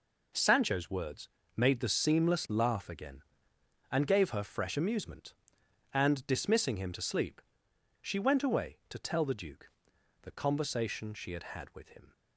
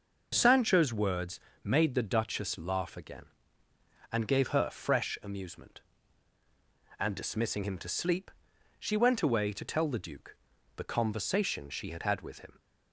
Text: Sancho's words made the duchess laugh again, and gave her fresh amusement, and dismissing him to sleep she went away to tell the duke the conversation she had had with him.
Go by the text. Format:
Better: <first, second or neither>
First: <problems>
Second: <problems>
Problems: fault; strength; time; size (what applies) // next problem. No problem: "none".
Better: second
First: pauses between "words" and "made"; slight; at 1.2 s; 0.28 s long // says "seamless" for "duchess"; at 1.8 s // pauses between "sleep" and "she"; noticeable; at 7.4 s; 0.62 s long // pauses between "duke" and "the"; noticeable; at 9.6 s; 0.54 s long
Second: pauses between "words" and "made"; slight; at 1.3 s; 0.24 s long // pauses between "sleep" and "she"; noticeable; at 8.3 s; 0.48 s long // pauses between "duke" and "the"; at 10.3 s; 0.42 s long